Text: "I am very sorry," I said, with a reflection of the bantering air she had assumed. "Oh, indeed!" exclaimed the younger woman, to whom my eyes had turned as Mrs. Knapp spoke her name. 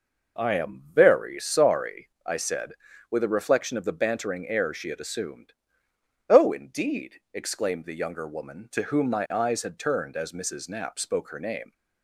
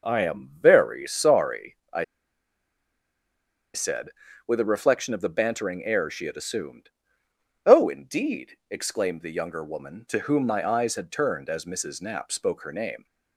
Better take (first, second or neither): first